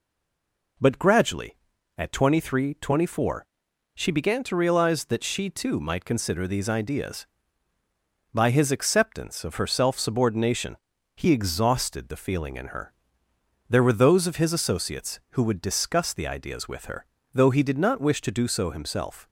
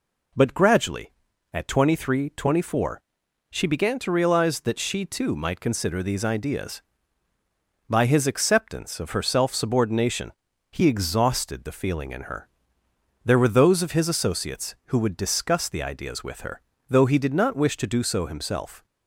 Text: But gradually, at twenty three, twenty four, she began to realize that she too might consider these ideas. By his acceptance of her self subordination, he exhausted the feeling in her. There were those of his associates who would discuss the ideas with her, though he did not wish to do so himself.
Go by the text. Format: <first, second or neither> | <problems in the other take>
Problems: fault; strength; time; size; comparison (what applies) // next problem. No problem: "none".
second | stays silent before the first word; slight; until 0.7 s; 0.7 s long